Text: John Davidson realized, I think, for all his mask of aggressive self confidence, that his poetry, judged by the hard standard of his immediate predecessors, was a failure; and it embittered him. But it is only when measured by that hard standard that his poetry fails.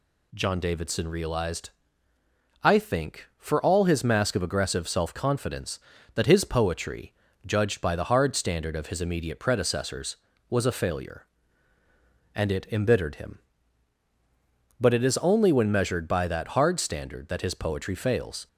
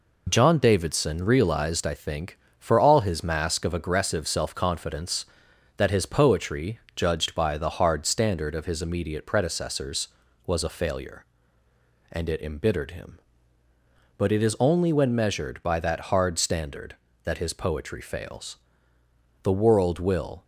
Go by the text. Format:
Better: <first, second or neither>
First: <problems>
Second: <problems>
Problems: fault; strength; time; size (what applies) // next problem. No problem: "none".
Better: first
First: none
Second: goes on to say "The world will"; noticeable; from 19.4 s on; 1.0 s long